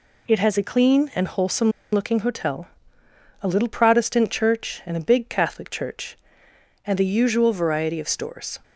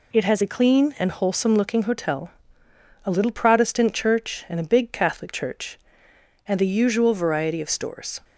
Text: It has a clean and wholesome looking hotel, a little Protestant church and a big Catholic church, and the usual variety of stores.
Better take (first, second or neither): second